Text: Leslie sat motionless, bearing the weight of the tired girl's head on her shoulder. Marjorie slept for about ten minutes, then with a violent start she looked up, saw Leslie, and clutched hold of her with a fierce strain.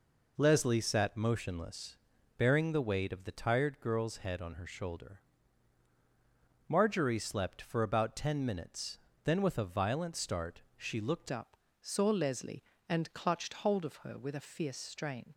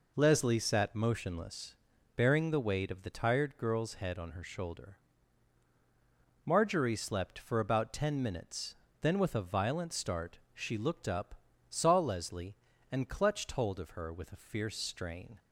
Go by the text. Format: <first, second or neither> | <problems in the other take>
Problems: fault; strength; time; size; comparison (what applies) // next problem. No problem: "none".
second | pauses between "start" and "she"; slight; at 10.5 s; 0.16 s long; slight in the second // changes voice at "up"; from 11.3 s on; 4.0 s long